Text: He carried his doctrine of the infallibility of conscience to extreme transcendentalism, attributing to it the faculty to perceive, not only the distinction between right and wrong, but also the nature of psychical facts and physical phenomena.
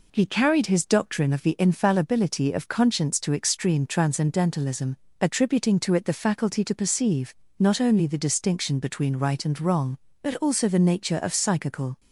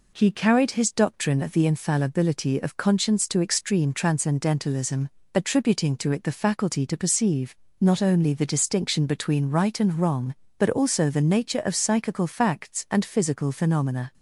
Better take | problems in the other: second | stops before "facts and physical phenomena"; at 11.9 s

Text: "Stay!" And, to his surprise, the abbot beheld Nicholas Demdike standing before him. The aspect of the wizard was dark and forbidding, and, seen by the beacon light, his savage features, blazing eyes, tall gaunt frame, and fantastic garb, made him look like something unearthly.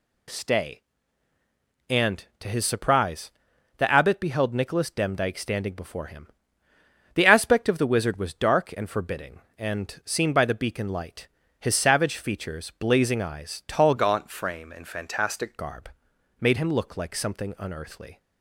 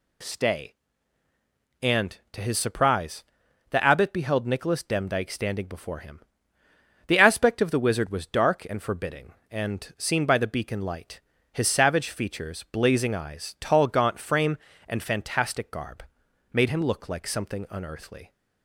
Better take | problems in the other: second | changes voice from "gaunt" to "fantastic"; from 13.9 to 15.5 s; 1.6 s long

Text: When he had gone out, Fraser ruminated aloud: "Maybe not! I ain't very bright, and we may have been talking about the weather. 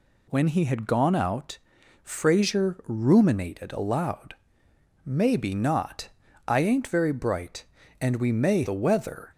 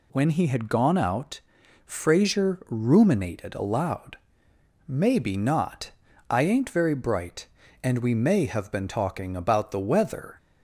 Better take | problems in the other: second | skips "have been talking about"; at 8.6 s

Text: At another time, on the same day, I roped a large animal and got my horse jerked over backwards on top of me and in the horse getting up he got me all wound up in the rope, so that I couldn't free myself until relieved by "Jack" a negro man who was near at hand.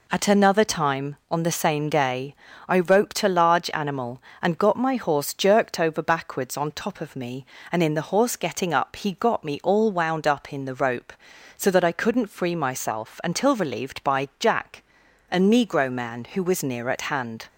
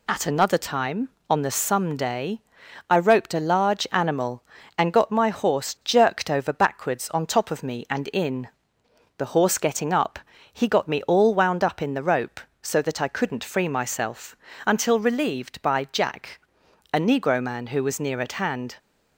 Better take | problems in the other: first | says "some" for "same"; at 1.5 s // pauses between "in" and "the"; noticeable; at 8.4 s; 0.70 s long // pauses between "up" and "he"; slight; at 10.1 s; 0.34 s long // pauses between "myself" and "until"; slight; at 14.3 s; 0.30 s long // pauses between "Jack" and "a"; noticeable; at 16.3 s; 0.52 s long; noticeable in the first

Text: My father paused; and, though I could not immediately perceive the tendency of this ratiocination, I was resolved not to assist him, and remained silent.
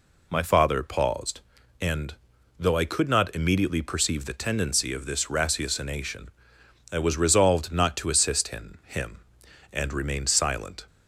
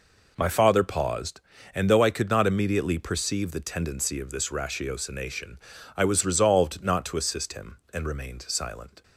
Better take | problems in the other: second | says "him" twice; at 8.8 s

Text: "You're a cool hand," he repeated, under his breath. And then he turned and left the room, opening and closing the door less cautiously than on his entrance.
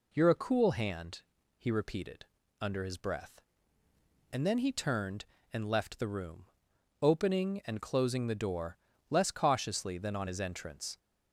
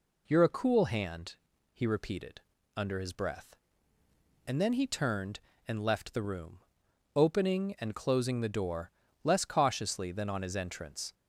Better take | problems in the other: neither | pauses between "door" and "less"; slight; the same in both

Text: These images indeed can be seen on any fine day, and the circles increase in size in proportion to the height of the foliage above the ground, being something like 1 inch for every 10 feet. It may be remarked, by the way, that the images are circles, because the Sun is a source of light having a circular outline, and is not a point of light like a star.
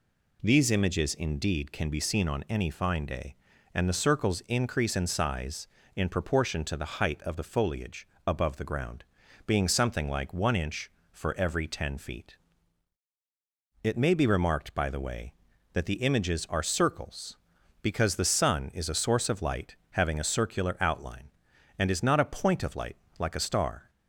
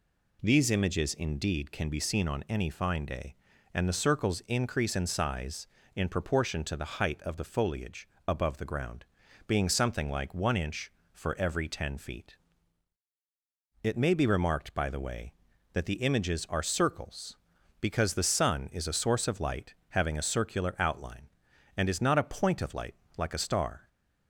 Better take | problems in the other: neither | pauses between "foliage" and "above"; slight; the same in both // pauses between "light" and "having"; slight; the same in both // pauses between "light" and "like"; slight; the same in both

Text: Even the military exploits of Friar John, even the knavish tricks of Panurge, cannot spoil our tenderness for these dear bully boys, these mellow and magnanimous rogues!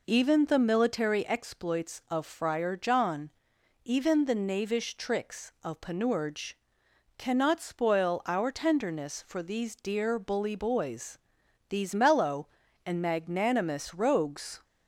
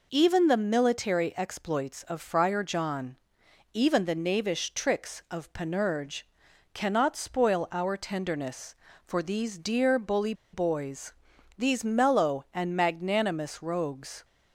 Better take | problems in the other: first | pauses between "bully" and "boys"; slight; at 10.3 s; 0.19 s long

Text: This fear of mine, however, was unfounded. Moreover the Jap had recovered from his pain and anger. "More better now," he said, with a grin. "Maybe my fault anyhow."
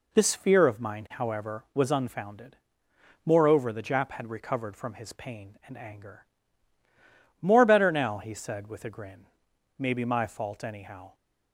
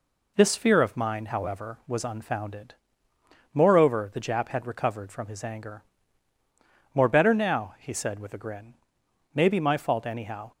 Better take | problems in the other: first | skips "pain and"; at 5.4 s

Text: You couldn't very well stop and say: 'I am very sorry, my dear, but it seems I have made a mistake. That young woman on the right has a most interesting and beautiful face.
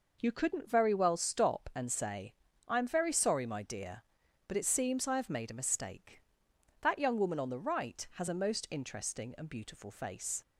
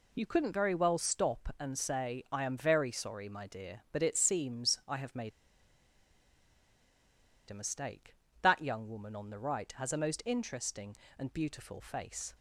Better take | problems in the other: first | pauses between "made" and "a"; strong; at 5.3 s; 2.1 s long

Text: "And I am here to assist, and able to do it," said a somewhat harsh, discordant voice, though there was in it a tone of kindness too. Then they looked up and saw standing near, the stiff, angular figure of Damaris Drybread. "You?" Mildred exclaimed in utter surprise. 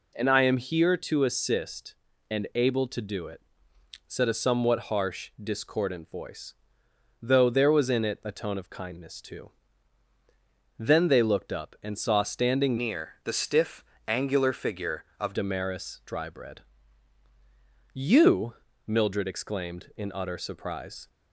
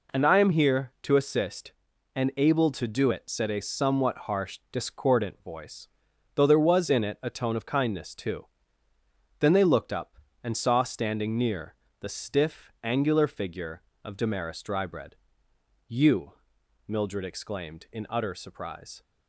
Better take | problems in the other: second | changes voice from "near" to "of"; from 12.7 to 15.3 s; 2.6 s long

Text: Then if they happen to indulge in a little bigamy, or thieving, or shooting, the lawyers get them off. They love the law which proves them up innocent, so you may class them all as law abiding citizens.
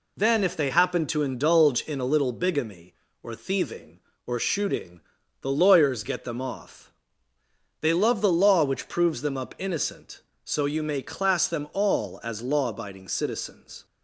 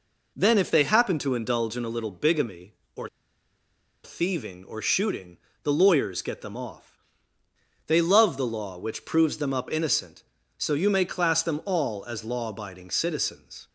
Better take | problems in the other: first | pauses between "or" and "thieving"; noticeable; at 3.0 s; 0.96 s long

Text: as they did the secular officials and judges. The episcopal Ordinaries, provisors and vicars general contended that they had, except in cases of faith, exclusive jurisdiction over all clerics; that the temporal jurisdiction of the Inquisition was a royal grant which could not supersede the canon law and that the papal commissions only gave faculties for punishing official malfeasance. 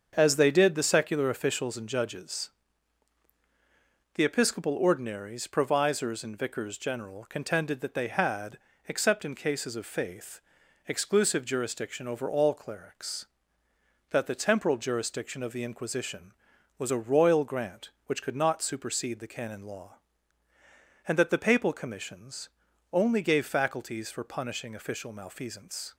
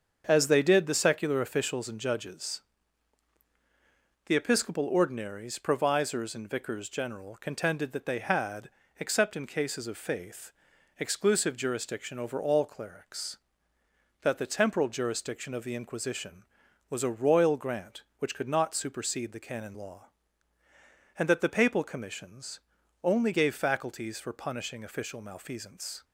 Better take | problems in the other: neither | starts louder than the rest; the same in both // pauses between "commissions" and "only"; noticeable; the same in both

